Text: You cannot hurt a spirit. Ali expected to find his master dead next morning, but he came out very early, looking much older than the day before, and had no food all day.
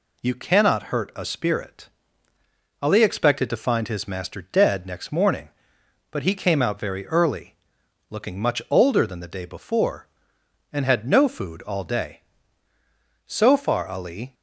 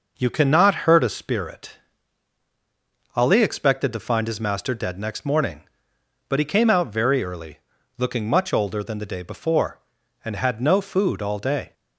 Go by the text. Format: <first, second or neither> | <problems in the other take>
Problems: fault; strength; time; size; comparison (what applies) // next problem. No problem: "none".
second | goes on to say "So far Ali"; noticeable; from 13.2 s on; 1.0 s long